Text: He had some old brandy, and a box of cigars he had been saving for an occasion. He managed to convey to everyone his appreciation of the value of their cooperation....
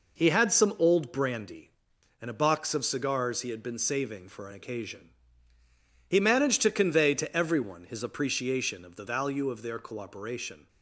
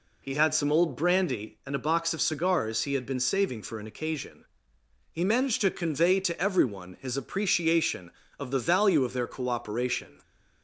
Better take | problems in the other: neither | none

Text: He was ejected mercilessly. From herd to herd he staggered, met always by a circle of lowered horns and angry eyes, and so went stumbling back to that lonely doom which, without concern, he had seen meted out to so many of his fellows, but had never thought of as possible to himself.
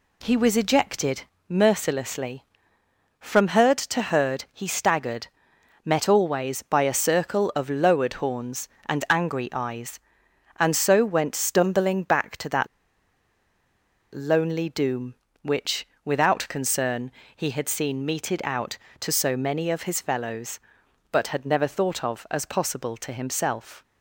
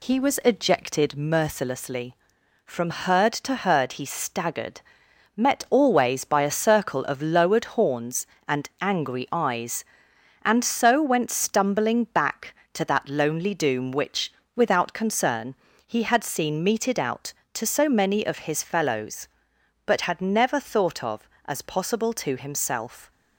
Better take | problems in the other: second | pauses between "ejected" and "mercilessly"; slight; at 1.2 s; 0.26 s long // pauses between "that" and "lonely"; strong; at 12.6 s; 1.4 s long

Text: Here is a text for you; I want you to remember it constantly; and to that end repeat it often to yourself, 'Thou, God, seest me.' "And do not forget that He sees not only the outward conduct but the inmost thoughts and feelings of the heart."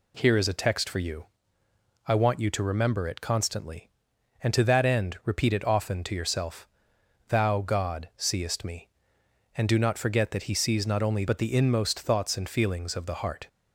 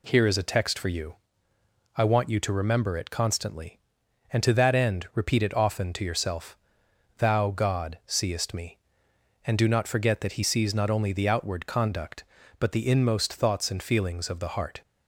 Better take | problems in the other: second | skips "the outward conduct"; at 11.2 s

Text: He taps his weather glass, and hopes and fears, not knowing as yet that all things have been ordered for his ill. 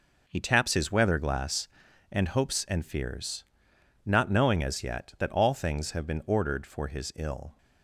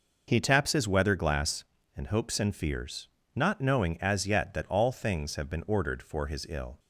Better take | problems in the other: neither | none

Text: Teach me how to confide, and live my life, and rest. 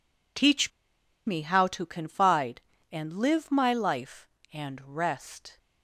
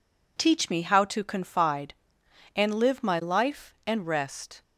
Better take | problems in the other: second | pauses between "Teach" and "me"; noticeable; at 0.7 s; 0.56 s long

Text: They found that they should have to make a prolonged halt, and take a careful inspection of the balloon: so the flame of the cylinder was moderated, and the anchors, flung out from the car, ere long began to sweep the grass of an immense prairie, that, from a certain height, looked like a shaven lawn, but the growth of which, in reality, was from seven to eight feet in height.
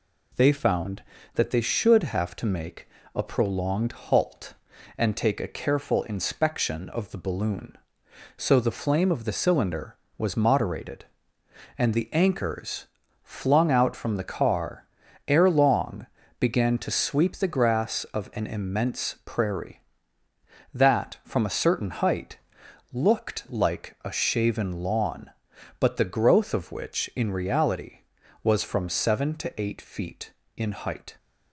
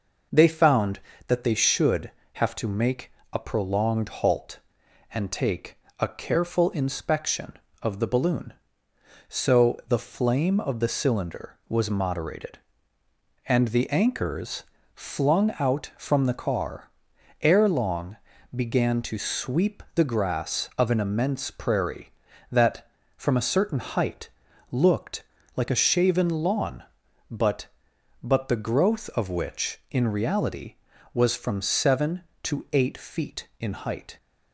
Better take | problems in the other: first | pauses between "make" and "a"; slight; at 3.1 s; 0.20 s long; slight in the first // pauses between "take" and "a"; slight; at 5.7 s; 0.22 s long // pauses between "long" and "began"; at 18.1 s; 0.38 s long; slight in the first // pauses between "looked" and "like"; slight; at 25.2 s; 0.32 s long // says "but" twice; at 28.2 s

